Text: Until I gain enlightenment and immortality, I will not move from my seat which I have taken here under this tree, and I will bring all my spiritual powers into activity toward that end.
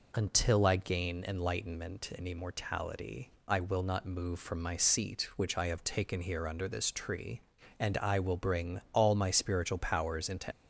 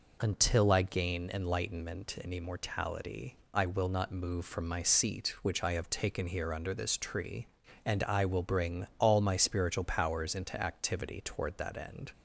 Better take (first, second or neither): second